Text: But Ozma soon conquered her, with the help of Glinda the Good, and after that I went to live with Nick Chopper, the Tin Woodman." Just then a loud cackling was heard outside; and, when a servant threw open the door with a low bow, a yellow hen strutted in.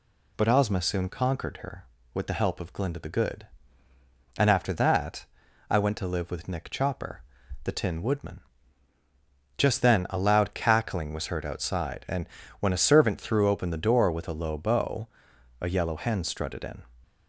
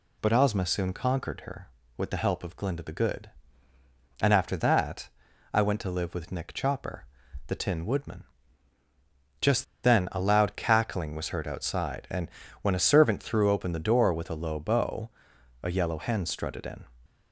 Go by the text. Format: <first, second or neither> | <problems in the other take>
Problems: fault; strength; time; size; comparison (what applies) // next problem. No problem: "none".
first | pauses between "that" and "I"; noticeable; at 5.0 s; 0.46 s long; noticeable in the first // pauses between "Just" and "then"; slight; at 9.6 s; 0.19 s long